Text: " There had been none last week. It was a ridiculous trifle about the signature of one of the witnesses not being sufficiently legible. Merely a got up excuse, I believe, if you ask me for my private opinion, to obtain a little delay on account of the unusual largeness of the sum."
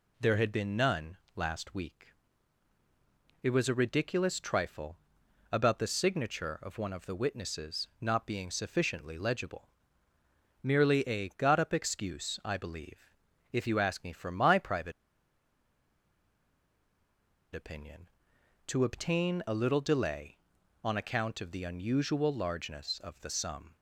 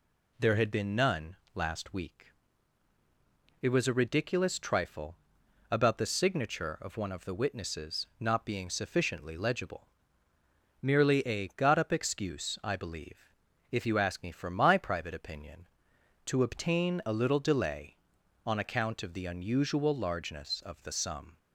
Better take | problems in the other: second | pauses between "none" and "last"; slight; at 1.1 s; 0.18 s long; slight in the second // pauses between "trifle" and "about"; noticeable; at 4.9 s; 0.56 s long; noticeable in the second // pauses between "private" and "opinion"; strong; at 14.9 s; 2.6 s long

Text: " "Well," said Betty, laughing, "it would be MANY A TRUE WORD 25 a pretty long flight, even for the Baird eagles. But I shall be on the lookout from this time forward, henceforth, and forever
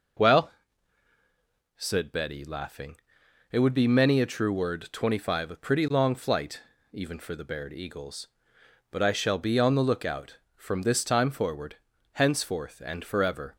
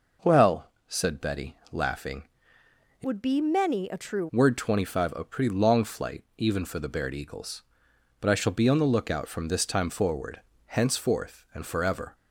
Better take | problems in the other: first | changes voice from "would" to "TRUE"; from 3.0 to 4.2 s; 1.2 s long

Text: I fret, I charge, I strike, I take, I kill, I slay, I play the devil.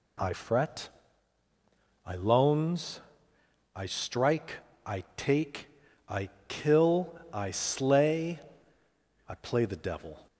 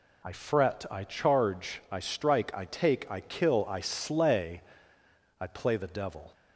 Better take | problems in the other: second | says "loans" for "charge"; at 2.1 s // pauses between "I" and "kill"; slight; at 6.2 s; 0.20 s long

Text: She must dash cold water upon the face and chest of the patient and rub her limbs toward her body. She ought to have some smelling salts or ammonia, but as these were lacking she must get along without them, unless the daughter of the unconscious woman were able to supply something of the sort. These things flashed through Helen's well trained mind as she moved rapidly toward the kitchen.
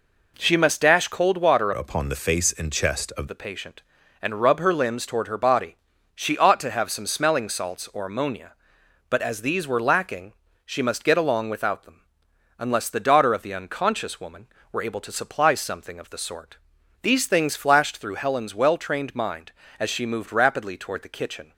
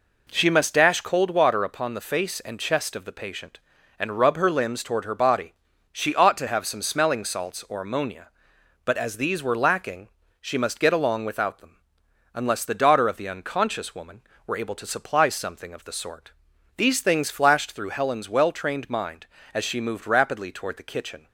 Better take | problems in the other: second | changes voice from "upon" to "of"; from 1.7 to 3.2 s; 1.5 s long // pauses between "lacking" and "she"; slight; at 10.3 s; 0.32 s long; slight in the second

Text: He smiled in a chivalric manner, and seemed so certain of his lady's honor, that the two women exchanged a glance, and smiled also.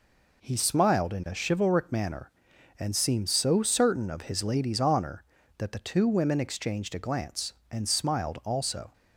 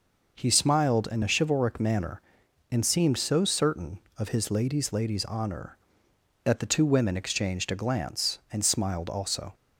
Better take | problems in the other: first | says "lady's" twice; at 4.9 s

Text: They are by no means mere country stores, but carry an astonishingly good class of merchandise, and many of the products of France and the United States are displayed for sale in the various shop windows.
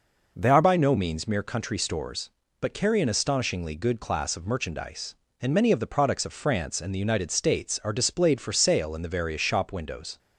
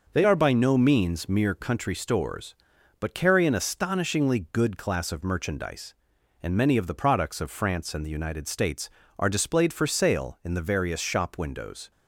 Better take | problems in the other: second | changes voice at "by"; from 0.6 s on; 9.5 s long

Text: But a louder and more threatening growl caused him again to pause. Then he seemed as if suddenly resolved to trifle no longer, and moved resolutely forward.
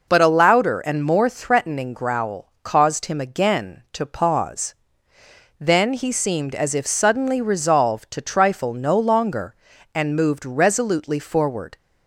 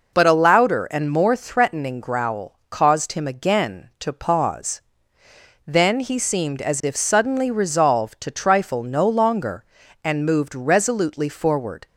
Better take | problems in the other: neither | none

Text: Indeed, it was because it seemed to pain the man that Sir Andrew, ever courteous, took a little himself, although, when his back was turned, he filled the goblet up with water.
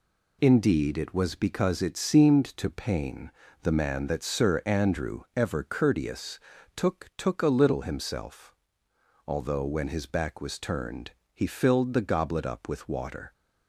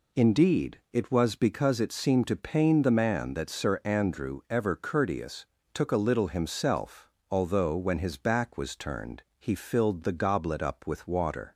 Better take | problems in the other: second | pauses between "pain" and "the"; slight; at 3.3 s; 0.32 s long // says "took" twice; at 7.1 s

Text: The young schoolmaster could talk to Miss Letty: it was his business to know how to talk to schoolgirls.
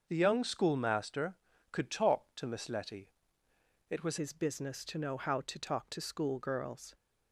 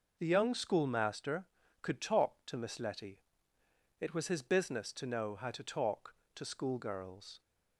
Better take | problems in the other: second | starts louder than the rest; until 1.0 s; 6.5 dB // changes voice at "his"; from 4.1 s on; 2.8 s long

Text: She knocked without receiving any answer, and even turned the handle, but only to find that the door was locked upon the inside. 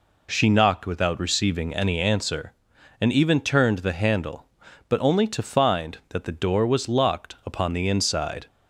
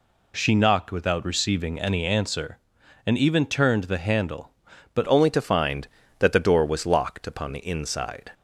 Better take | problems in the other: first | changes voice at "only"; from 5.0 s on; 3.3 s long

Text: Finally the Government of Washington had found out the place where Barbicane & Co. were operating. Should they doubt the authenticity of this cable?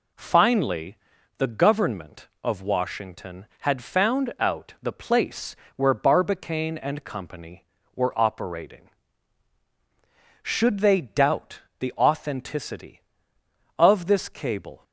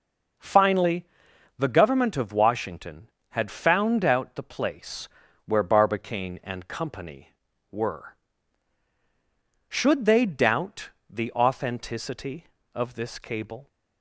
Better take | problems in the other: first | pauses between "Finally" and "the"; noticeable; at 1.0 s; 0.54 s long; also in the first // pauses between "place" and "where"; at 5.0 s; 0.38 s long; slight in the first // skips "operating"; at 8.9 s // pauses between "doubt" and "the"; slight; at 10.8 s; 0.20 s long; slight in the first

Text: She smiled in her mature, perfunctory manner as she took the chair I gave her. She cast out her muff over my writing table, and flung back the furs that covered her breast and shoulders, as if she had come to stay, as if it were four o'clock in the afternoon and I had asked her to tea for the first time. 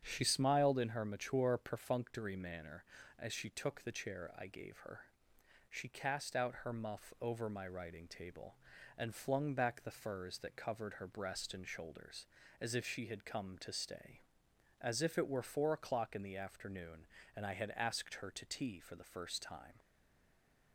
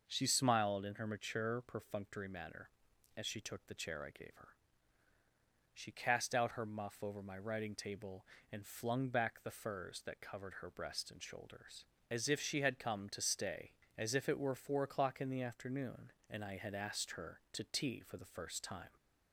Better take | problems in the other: second | starts louder than the rest; strong; until 1.0 s; 7.5 dB // stays silent after the last word; slight; from 19.7 s on; 1.0 s long

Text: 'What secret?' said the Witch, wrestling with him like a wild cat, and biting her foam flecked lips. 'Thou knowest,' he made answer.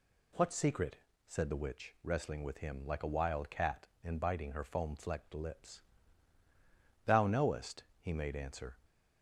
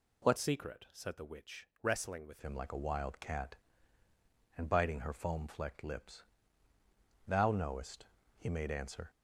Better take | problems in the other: first | changes voice from "secret" to "with"; from 0.3 to 2.3 s; 2.0 s long

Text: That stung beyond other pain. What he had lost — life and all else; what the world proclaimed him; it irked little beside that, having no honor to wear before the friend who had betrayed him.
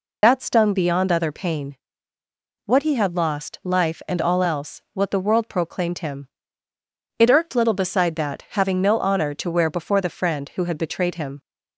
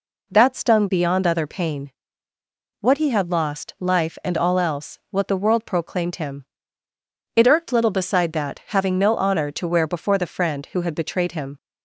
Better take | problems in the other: second | loses the start of "That"; at 0.2 s; 70 ms

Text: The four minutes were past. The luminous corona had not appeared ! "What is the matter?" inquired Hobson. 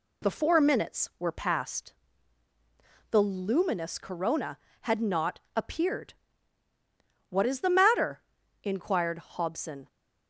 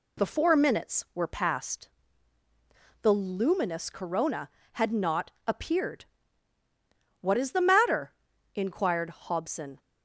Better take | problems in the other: neither | pauses between "not" and "appeared"; slight; the same in both

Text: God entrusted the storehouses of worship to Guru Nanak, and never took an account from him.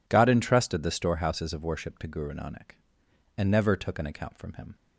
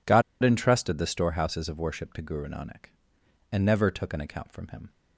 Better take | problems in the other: first | pauses between "God" and "entrusted"; slight; at 0.2 s; 0.21 s long

